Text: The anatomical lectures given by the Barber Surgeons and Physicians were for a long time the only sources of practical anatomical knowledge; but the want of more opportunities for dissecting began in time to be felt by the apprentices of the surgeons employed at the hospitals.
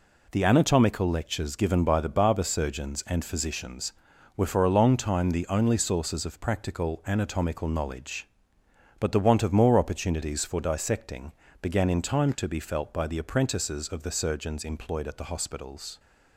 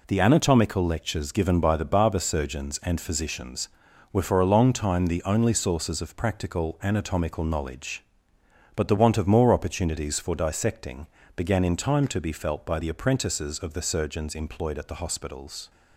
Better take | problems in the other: neither | pauses between "dissecting" and "began"; slight; the same in both

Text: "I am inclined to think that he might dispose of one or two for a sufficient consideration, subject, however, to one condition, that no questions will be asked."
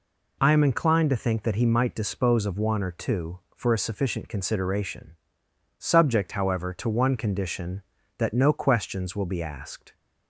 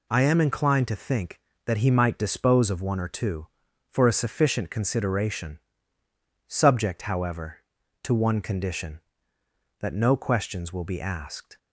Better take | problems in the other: neither | none

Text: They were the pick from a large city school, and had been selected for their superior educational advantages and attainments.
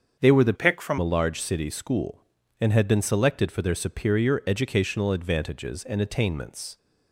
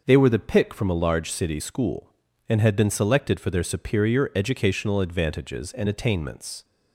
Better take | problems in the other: second | starts louder than the rest; until 1.2 s; 7 dB // changes voice from "pick" to "from"; from 0.5 to 0.9 s; 0.4 s long

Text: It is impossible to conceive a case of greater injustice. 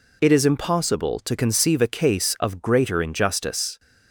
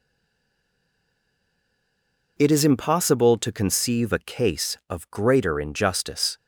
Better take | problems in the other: first | stays silent before the first word; until 2.3 s; 2.3 s long

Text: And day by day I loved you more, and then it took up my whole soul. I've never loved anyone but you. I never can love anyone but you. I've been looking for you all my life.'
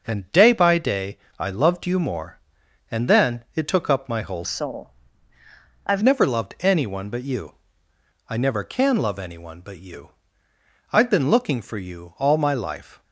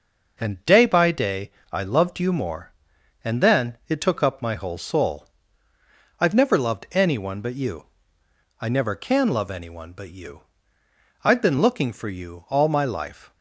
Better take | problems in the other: second | pauses between "day" and "I"; slight; at 1.1 s; 0.22 s long; slight in the second // changes voice from "soul" to "I've"; from 4.4 to 6.0 s; 1.6 s long

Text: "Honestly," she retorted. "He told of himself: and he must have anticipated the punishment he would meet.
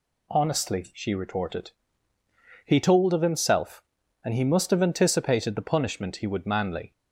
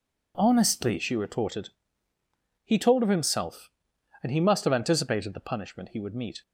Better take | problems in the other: second | says "manly" for "meet"; at 6.4 s

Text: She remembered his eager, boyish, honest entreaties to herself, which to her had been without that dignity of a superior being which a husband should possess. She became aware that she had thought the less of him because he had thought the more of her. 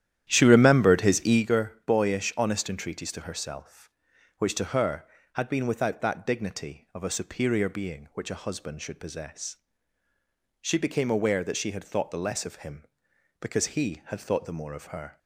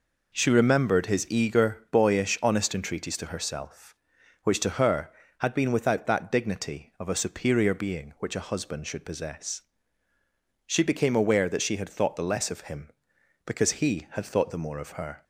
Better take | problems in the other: second | starts louder than the rest; strong; until 1.5 s; 11 dB

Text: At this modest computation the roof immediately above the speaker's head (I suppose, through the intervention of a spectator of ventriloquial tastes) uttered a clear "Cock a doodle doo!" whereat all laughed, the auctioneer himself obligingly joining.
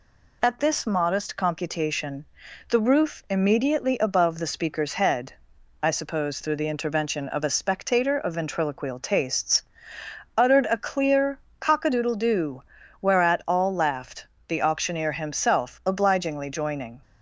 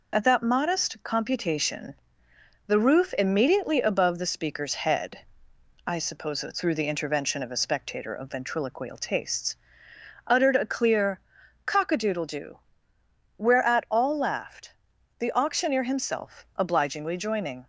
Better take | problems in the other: first | says "that" for "this"; at 0.2 s // pauses between "computation" and "the"; noticeable; at 1.9 s; 0.72 s long; noticeable in the first // pauses between "clear" and "Cock"; noticeable; at 11.1 s; 0.48 s long; slight in the first

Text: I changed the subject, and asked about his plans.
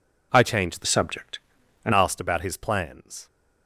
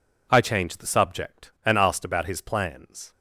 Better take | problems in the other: second | changes voice from "subject" to "and"; from 0.8 to 1.9 s; 1.1 s long

